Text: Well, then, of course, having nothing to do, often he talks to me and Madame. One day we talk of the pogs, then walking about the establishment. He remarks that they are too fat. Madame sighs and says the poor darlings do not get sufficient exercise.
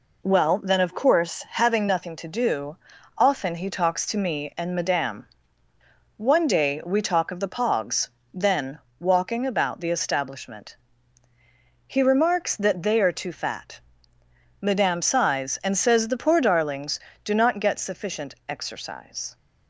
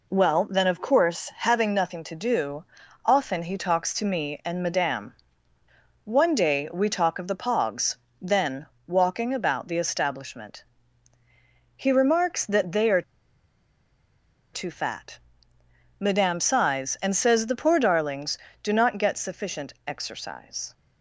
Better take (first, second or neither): first